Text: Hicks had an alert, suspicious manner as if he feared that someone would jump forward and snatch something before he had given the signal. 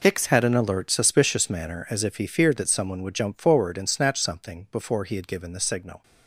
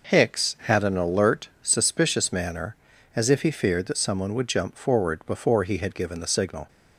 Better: first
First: none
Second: skips "and snatch something"; at 5.2 s

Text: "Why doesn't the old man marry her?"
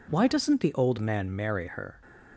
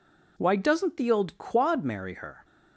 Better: first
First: none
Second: says "quad" for "man"; at 1.3 s

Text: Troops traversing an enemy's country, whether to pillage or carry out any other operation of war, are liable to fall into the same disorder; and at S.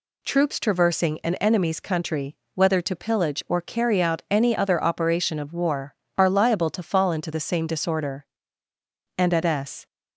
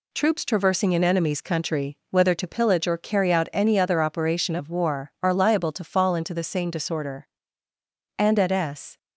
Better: first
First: none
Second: gets quieter; noticeable; throughout; 5.5 dB

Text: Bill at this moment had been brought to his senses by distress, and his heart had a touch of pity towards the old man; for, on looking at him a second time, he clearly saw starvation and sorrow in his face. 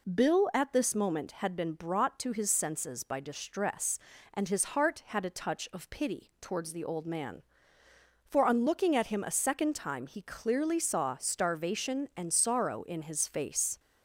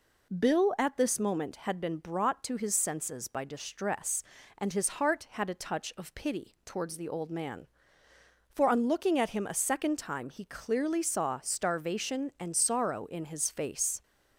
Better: neither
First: none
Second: none

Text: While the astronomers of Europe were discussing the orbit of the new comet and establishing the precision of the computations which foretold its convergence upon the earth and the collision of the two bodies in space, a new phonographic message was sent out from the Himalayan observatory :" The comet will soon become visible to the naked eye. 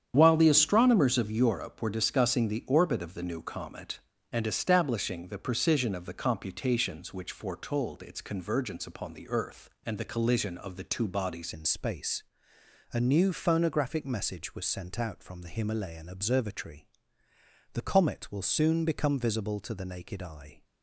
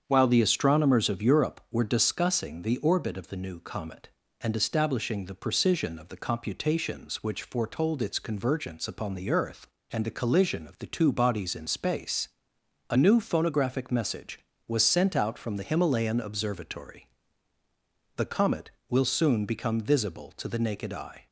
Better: second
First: starts louder than the rest; strong; until 1.1 s; 8.5 dB // changes voice at "in"; from 11.5 s on; 9.1 s long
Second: starts louder than the rest; strong; until 1.0 s; 7.5 dB

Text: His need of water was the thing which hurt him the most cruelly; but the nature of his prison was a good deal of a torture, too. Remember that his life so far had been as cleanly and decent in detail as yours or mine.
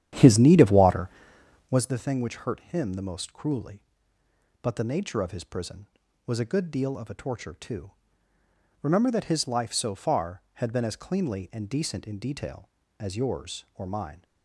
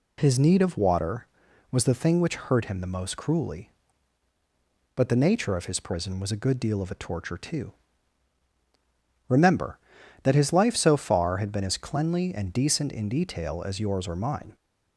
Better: second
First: starts louder than the rest; strong; until 1.9 s; 10.5 dB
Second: none

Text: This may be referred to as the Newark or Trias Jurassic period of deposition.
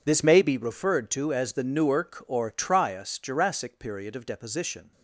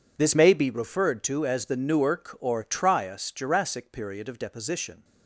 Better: neither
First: none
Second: none

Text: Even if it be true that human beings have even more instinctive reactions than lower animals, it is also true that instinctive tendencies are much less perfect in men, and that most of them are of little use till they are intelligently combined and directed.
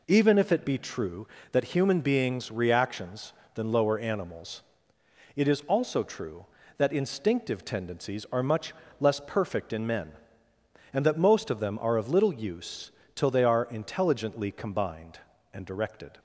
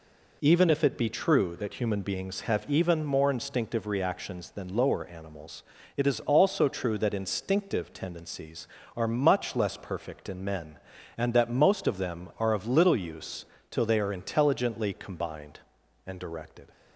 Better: second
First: skips "have even more instinctive"; at 2.5 s // pauses between "much" and "less"; slight; at 8.7 s; 0.26 s long // pauses between "use" and "till"; slight; at 12.9 s; 0.24 s long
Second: pauses between "use" and "till"; slight; at 13.4 s; 0.24 s long

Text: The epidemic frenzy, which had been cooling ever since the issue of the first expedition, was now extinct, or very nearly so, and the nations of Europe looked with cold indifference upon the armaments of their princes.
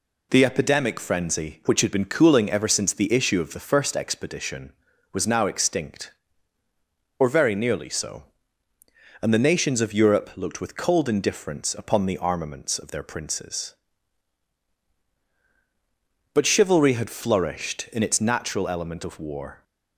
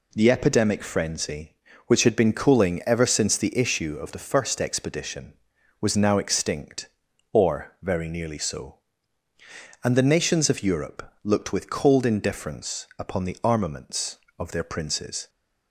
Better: second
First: goes on to say "But chivalry had flourished in its natural element of war"; strong; from 16.3 s on; 3.2 s long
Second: none

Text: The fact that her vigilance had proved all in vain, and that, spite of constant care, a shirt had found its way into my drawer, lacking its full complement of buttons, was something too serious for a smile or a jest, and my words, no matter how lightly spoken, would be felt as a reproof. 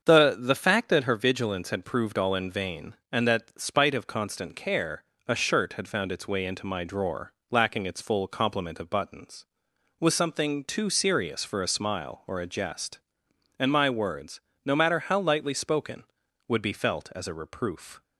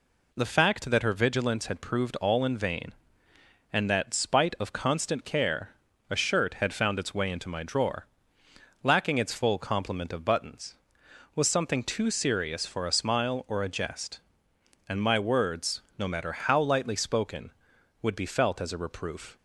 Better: second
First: starts louder than the rest; until 1.0 s; 7 dB // says "The" twice; at 0.3 s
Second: none

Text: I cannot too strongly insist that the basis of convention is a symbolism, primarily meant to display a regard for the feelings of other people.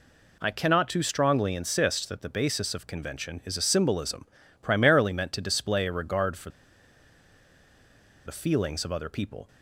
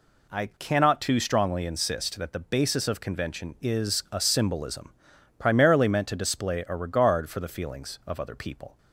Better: second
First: pauses between "for" and "the"; strong; at 6.5 s; 1.7 s long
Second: none

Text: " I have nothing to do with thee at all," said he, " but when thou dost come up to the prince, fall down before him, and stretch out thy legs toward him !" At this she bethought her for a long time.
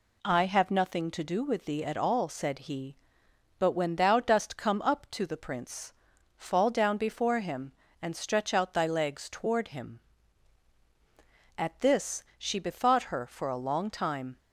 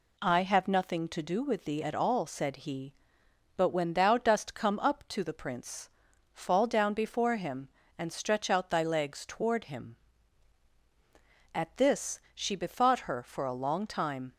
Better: neither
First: none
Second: none

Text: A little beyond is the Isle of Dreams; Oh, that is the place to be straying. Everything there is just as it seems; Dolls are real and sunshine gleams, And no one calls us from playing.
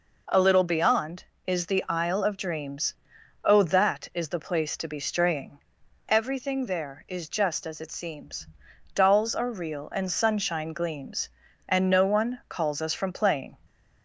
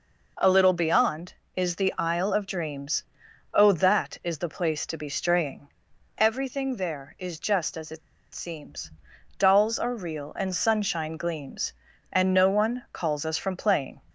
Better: first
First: none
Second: pauses between "it" and "seems"; slight; at 8.0 s; 0.34 s long

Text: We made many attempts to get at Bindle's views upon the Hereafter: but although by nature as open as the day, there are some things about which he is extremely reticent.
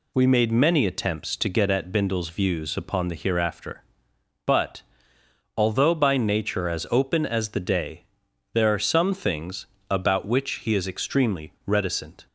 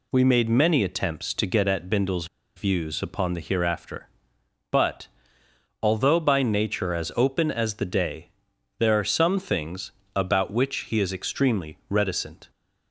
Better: first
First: pauses between "but" and "although"; noticeable; at 4.8 s; 0.74 s long // pauses between "things" and "about"; slight; at 9.6 s; 0.24 s long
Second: pauses between "Bindle's" and "views"; slight; at 2.2 s; 0.30 s long // pauses between "but" and "although"; noticeable; at 5.0 s; 0.74 s long // pauses between "things" and "about"; slight; at 9.8 s; 0.24 s long

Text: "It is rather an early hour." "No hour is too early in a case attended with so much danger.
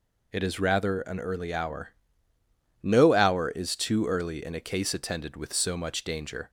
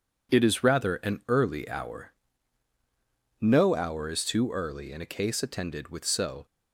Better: first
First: none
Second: stops before "much danger"; at 6.4 s

